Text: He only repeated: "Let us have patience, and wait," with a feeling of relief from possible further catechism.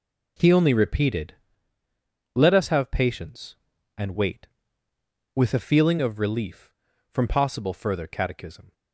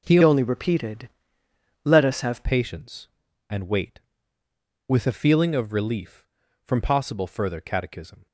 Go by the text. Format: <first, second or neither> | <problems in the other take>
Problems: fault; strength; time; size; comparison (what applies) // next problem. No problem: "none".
first | changes voice from "only" to "have"; from 0.2 to 2.4 s; 2.2 s long